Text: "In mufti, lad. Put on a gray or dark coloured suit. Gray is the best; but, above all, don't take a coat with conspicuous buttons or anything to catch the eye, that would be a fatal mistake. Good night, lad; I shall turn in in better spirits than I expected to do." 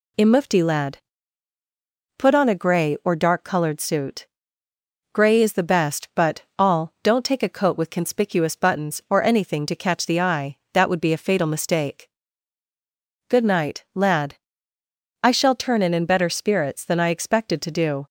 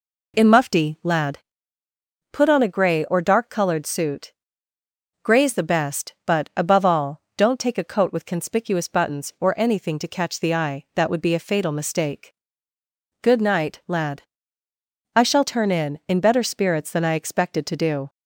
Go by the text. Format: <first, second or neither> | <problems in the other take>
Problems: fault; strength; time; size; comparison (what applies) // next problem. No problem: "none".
second | skips "above"; at 6.4 s